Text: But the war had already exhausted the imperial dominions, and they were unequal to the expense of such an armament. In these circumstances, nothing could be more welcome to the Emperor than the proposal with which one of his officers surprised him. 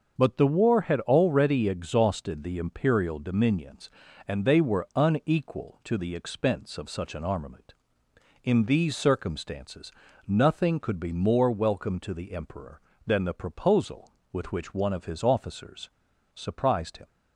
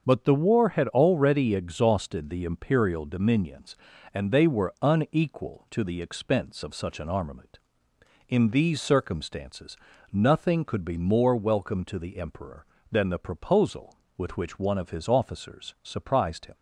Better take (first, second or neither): second